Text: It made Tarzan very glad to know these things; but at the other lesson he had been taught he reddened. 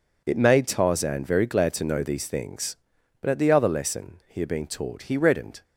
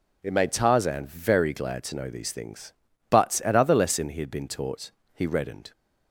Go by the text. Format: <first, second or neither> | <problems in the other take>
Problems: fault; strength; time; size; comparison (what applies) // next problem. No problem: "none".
first | skips "the"; at 3.5 s // pauses between "taught" and "he"; slight; at 4.9 s; 0.22 s long